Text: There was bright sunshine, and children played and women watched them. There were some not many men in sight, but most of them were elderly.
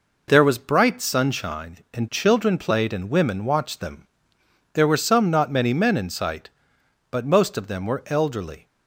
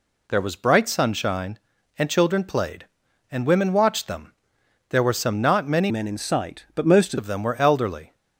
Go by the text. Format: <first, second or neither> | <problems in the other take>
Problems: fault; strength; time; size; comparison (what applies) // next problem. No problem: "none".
first | changes voice from "men" to "most"; from 5.8 to 7.1 s; 1.3 s long